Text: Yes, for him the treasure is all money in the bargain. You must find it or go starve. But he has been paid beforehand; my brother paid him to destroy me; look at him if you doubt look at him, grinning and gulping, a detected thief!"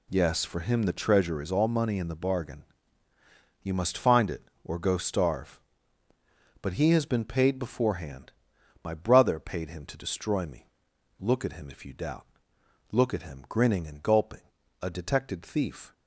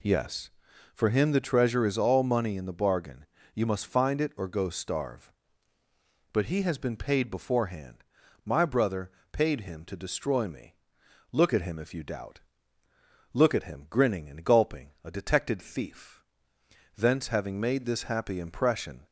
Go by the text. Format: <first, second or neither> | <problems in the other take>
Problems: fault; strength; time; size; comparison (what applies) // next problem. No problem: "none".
first | pauses between "brother" and "paid"; slight; at 9.1 s; 0.20 s long // pauses between "doubt" and "look"; noticeable; at 12.3 s; 0.92 s long; noticeable in the first // goes on to say "Thence having made this happy impression"; strong; from 16.9 s on; 2.0 s long